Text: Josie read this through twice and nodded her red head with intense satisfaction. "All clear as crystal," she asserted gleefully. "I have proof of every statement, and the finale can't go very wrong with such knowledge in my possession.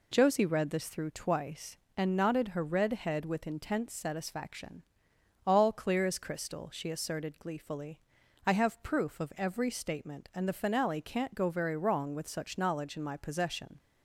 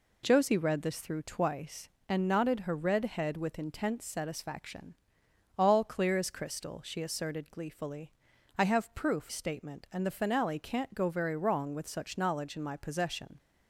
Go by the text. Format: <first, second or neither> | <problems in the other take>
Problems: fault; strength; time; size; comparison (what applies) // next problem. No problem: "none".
first | skips "of every"; at 9.2 s